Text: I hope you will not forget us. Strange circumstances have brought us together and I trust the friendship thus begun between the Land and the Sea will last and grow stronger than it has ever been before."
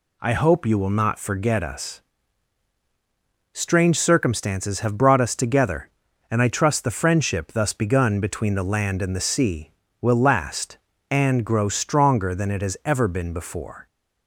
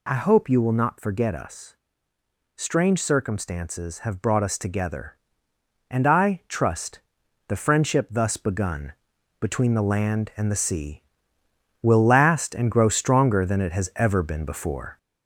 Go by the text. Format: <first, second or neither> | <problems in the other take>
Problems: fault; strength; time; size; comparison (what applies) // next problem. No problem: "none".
first | gets louder; throughout; 3.5 dB // pauses between "trust" and "the"; noticeable; at 6.9 s; 0.50 s long // pauses between "begun" and "between"; noticeable; at 8.9 s; 0.48 s long